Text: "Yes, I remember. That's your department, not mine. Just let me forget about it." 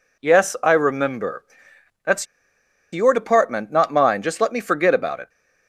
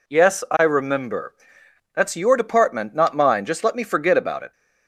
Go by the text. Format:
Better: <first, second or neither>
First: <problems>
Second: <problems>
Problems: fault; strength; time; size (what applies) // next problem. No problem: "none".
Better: second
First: pauses between "That's" and "your"; noticeable; at 2.2 s; 0.66 s long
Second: none